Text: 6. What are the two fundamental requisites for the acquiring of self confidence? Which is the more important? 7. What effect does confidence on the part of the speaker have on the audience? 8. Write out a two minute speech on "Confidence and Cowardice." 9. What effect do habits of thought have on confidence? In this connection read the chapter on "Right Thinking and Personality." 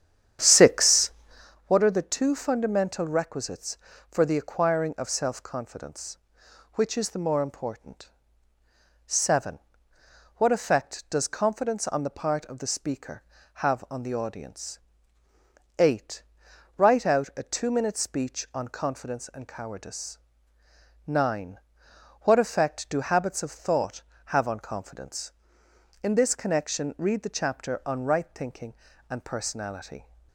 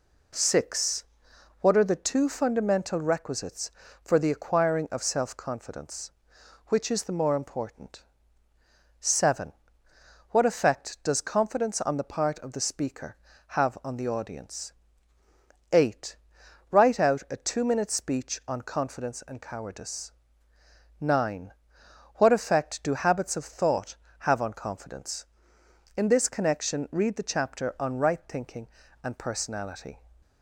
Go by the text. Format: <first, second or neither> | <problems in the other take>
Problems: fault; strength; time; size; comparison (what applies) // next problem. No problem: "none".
second | starts louder than the rest; strong; until 1.6 s; 9 dB